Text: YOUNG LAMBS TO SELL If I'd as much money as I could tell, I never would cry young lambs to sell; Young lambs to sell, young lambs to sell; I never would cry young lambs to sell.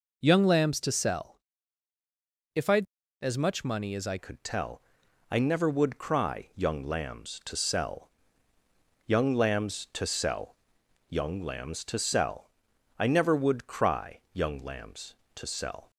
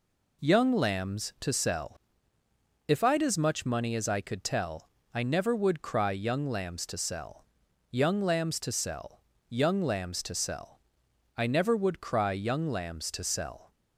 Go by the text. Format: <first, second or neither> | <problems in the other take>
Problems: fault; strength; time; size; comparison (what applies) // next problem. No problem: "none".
second | pauses between "SELL" and "If"; at 1.3 s; 1.1 s long; noticeable in the second // changes voice at "could"; from 4.1 s on; 11.8 s long